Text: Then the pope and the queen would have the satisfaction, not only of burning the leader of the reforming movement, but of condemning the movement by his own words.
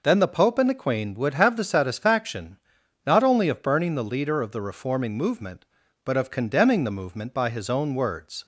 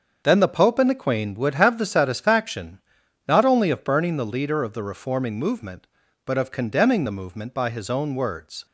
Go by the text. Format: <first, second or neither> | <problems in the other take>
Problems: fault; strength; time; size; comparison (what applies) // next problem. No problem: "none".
first | gets quieter; strong; throughout; 9 dB